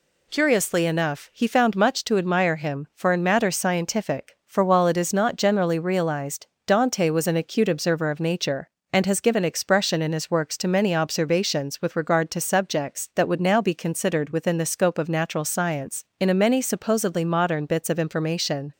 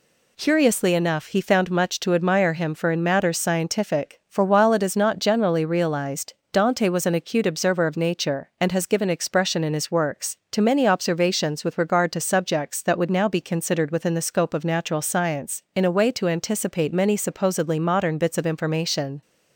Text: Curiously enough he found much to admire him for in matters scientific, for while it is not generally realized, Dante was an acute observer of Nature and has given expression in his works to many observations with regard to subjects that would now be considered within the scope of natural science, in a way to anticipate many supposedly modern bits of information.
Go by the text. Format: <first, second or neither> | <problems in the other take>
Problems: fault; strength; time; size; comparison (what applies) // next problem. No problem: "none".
second | skips "way to anticipate"; at 16.3 s